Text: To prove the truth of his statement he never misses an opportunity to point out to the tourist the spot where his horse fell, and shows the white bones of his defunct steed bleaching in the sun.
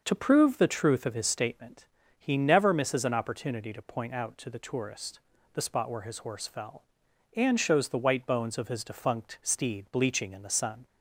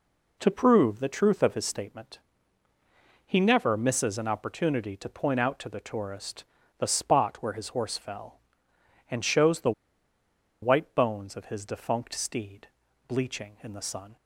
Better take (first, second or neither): first